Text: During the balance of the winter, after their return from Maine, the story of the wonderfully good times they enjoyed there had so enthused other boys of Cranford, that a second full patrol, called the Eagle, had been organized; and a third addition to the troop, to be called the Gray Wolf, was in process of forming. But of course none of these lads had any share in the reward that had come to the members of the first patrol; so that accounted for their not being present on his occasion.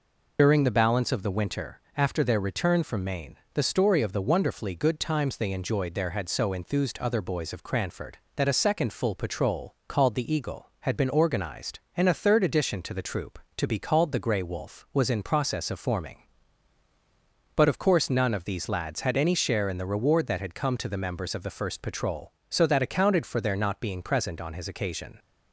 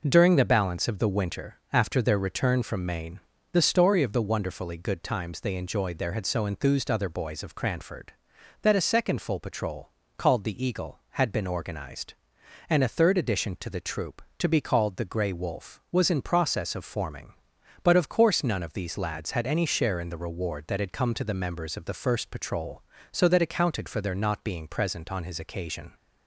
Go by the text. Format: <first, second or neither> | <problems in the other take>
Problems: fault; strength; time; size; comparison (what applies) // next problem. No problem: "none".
second | loses the start of "During"; at 0.3 s; 75 ms